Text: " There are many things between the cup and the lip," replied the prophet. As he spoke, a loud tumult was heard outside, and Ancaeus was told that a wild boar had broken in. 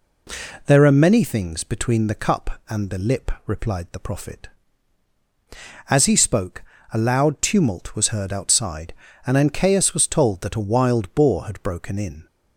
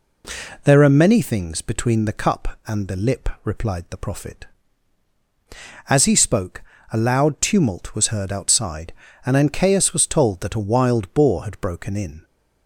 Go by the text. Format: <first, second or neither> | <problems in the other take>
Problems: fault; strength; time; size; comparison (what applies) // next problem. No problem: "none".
neither | none